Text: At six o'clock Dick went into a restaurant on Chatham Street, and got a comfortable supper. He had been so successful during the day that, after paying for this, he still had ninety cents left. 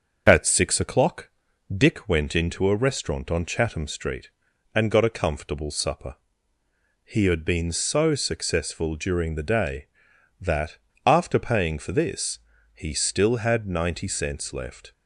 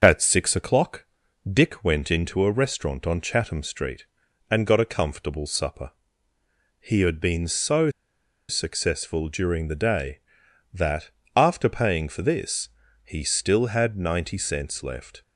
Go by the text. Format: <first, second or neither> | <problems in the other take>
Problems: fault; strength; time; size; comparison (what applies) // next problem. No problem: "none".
first | starts louder than the rest; until 1.0 s; 6.5 dB; also in the first // pauses between "o'clock" and "Dick"; at 1.0 s; 0.44 s long; also in the first // pauses between "so" and "successful"; noticeable; at 7.8 s; 0.59 s long